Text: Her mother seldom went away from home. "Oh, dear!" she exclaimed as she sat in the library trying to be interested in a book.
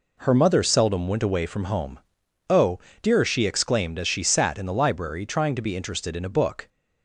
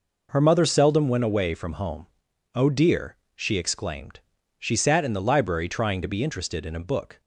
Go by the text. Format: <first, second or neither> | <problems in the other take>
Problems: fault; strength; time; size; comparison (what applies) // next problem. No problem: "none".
first | skips "as"; at 4.3 s